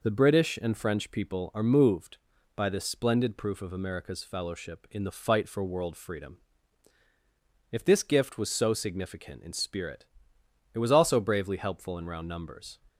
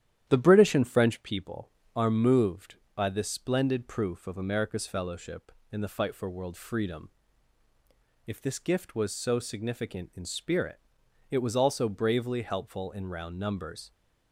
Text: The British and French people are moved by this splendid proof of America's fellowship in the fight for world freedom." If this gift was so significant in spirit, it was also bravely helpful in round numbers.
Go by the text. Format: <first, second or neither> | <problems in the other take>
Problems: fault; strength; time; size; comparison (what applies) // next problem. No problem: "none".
first | starts louder than the rest; strong; until 1.4 s; 11 dB